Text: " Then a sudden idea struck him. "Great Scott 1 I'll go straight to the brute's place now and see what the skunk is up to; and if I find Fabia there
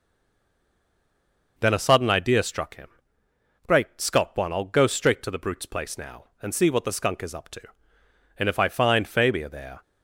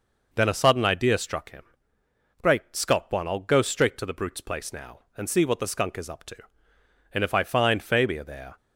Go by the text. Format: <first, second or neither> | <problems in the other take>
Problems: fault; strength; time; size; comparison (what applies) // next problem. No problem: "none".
second | stays silent before the first word; noticeable; until 1.5 s; 1.5 s long